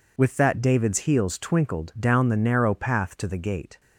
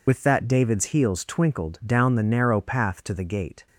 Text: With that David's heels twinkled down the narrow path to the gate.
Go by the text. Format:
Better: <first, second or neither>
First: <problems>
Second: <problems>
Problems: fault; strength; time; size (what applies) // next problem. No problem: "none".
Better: first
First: none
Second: loses the start of "With"; at 0.0 s; 35 ms